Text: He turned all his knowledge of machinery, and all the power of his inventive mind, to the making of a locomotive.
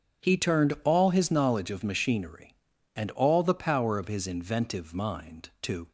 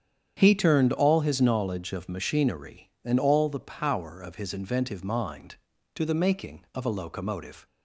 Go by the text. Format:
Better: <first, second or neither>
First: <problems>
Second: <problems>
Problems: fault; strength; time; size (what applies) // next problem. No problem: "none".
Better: second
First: starts louder than the rest; strong; until 1.3 s; 8.5 dB // stops before "the making of a locomotive"; at 5.8 s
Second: starts louder than the rest; strong; until 1.3 s; 8.5 dB